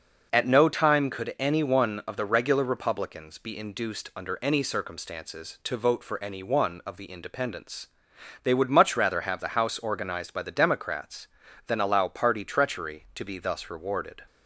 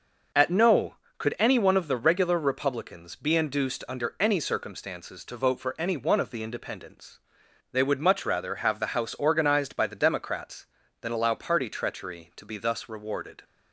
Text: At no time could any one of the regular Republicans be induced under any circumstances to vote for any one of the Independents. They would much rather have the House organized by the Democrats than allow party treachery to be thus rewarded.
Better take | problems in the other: first | skips "time"; at 1.0 s

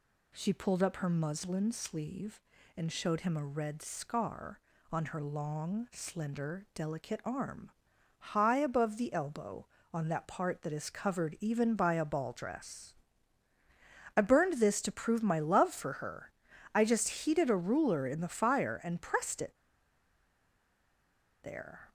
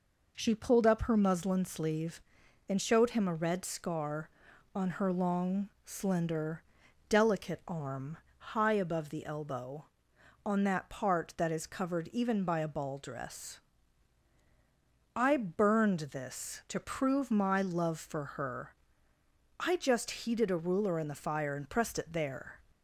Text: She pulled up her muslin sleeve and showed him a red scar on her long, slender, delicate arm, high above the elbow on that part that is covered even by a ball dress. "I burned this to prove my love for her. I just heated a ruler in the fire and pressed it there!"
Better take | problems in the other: second | pauses between "it" and "there"; strong; at 19.5 s; 1.9 s long

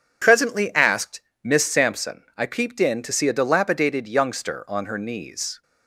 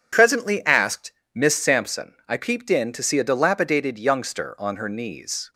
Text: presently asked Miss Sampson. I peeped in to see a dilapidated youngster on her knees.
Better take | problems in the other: neither | pauses between "asked" and "Miss"; slight; the same in both

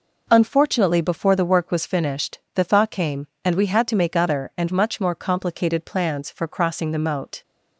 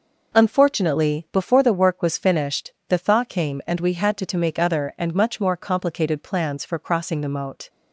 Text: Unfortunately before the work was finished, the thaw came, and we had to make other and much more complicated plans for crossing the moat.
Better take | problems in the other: first | says "to" twice; at 4.2 s

